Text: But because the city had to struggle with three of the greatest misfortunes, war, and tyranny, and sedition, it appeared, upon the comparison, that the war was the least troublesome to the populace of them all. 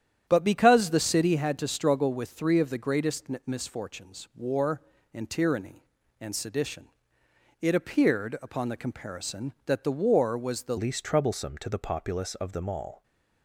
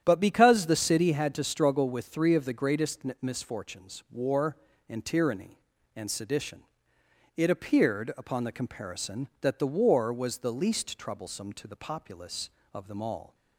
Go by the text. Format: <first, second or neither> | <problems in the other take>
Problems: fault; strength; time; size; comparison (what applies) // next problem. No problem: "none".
second | starts louder than the rest; strong; until 1.2 s; 9.5 dB; strong in the second // pauses between "greatest" and "misfortunes"; slight; at 3.2 s; 0.18 s long; slight in the second // changes voice at "least"; from 10.7 s on; 2.3 s long